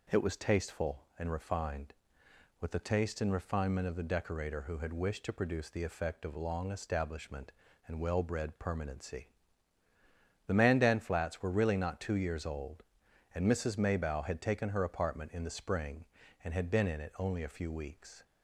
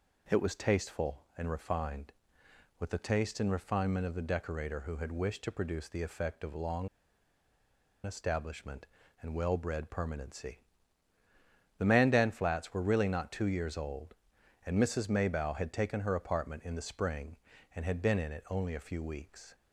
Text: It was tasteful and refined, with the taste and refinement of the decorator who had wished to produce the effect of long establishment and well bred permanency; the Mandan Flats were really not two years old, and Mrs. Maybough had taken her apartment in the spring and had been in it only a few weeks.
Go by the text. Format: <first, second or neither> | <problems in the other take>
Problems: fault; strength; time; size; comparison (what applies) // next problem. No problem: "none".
first | pauses between "long" and "establishment"; at 6.8 s; 1.1 s long